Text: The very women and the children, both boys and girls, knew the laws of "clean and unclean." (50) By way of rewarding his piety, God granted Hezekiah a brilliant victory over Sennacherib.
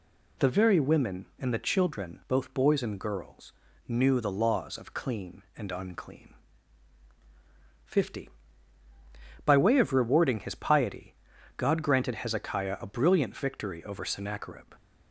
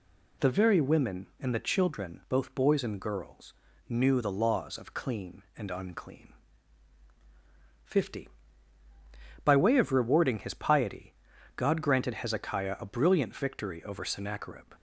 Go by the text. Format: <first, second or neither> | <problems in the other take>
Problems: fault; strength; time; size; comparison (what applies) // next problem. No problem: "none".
neither | none